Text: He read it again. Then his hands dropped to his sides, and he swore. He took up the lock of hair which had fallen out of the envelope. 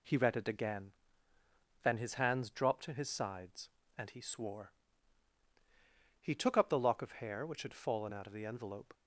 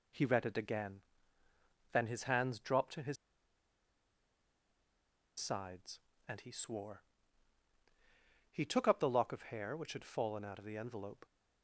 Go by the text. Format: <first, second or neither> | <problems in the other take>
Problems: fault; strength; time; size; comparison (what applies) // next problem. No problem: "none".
first | pauses between "his" and "sides"; strong; at 3.1 s; 2.2 s long